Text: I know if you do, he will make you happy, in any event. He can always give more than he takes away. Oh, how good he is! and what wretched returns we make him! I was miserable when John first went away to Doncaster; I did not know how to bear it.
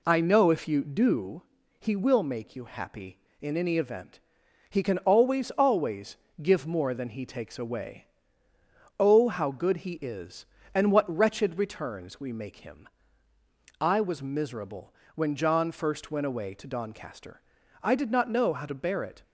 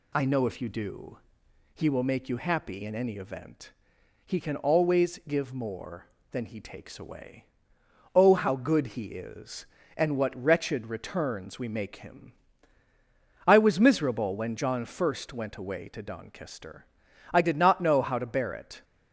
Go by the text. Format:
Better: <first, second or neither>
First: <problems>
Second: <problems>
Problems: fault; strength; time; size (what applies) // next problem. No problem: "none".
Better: second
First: says "always" twice; at 5.5 s // pauses between "miserable" and "when"; slight; at 14.9 s; 0.22 s long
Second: none